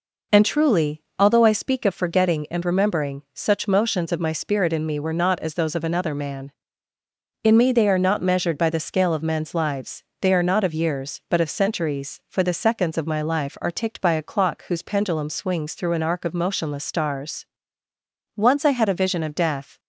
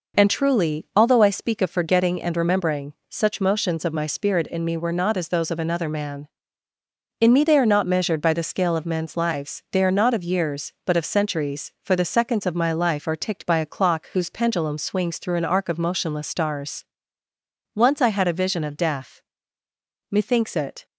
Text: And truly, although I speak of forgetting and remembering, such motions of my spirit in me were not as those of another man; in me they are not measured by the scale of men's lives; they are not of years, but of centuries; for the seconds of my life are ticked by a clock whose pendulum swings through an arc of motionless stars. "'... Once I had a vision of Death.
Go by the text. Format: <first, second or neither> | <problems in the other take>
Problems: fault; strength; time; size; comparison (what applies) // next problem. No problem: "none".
first | goes on to say "Methinks it"; noticeable; from 20.0 s on; 0.76 s long